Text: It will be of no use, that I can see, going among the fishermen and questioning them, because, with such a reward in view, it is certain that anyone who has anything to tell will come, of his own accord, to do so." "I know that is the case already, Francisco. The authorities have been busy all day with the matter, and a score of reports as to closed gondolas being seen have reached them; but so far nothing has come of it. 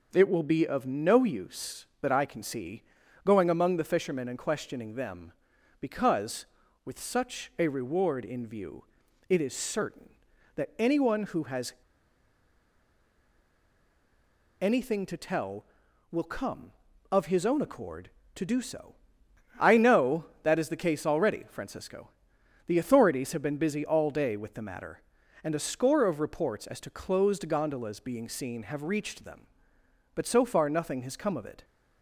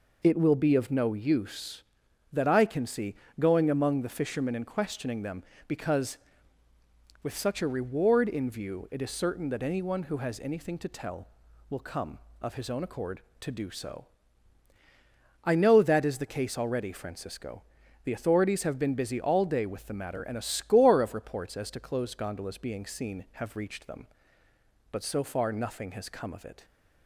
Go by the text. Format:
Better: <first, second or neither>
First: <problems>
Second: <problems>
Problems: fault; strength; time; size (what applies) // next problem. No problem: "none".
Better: second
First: pauses between "has" and "anything"; strong; at 11.7 s; 2.8 s long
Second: none